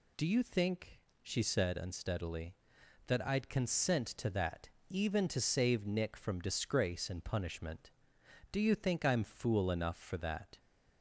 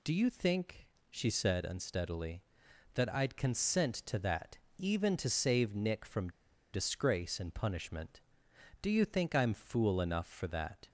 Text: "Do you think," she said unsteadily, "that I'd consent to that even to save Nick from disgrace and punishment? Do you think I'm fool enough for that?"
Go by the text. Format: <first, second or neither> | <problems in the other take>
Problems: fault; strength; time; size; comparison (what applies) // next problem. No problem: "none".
first | pauses between "that" and "even"; slight; at 4.5 s; 0.20 s long; slight in the first // pauses between "from" and "disgrace"; at 6.3 s; 0.41 s long